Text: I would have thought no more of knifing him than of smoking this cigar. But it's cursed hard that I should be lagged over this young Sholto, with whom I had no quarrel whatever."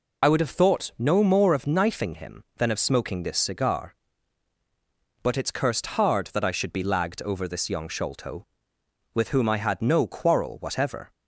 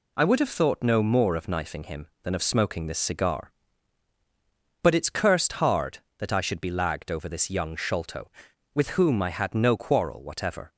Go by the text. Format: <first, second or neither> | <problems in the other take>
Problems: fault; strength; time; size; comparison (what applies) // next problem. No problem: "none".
second | loses the start of "I"; at 0.2 s; 45 ms